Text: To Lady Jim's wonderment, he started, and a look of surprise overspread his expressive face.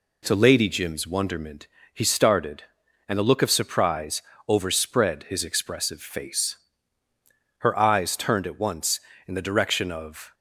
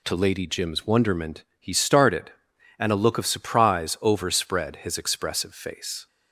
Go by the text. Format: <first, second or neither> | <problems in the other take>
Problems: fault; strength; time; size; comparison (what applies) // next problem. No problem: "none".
second | pauses between "surprise" and "overspread"; slight; at 4.2 s; 0.26 s long // goes on to say "Her eyes turned at once in the direction of"; strong; from 7.5 s on; 2.7 s long